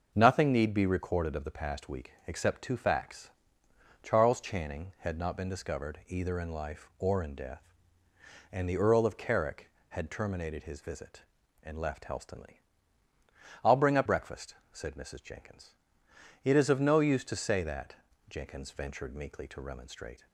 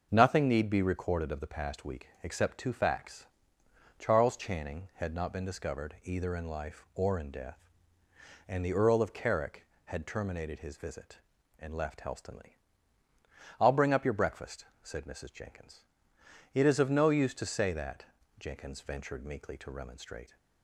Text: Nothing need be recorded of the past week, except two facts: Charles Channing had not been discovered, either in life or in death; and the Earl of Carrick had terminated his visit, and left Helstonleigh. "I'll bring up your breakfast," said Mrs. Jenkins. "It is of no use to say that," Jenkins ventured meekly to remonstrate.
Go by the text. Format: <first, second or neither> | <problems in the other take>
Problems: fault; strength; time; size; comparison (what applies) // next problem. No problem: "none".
second | starts louder than the rest; noticeable; until 1.1 s; 6 dB; noticeable in the second // skips "your"; at 14.0 s